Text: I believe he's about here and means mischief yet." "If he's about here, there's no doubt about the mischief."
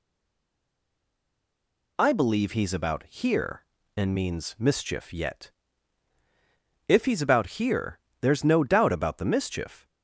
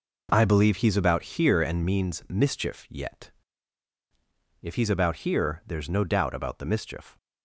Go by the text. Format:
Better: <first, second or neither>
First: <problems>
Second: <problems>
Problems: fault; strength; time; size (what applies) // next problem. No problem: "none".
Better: second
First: stays silent before the first word; noticeable; until 1.9 s; 1.9 s long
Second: none